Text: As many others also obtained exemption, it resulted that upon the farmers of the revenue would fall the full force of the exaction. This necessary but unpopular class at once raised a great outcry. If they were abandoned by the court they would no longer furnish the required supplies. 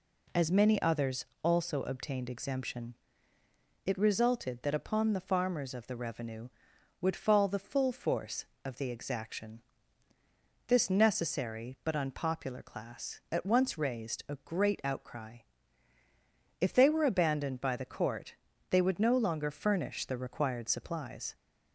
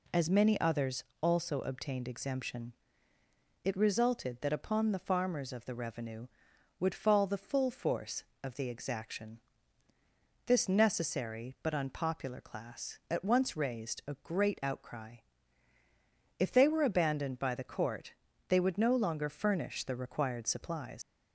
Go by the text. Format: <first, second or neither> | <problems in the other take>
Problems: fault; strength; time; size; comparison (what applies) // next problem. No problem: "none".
first | pauses between "others" and "also"; slight; at 1.0 s; 0.18 s long; slight in the first // pauses between "court" and "they"; slight; at 18.1 s; 0.36 s long; slight in the first // leaves "supplies" unfinished; at 21.0 s; 110 ms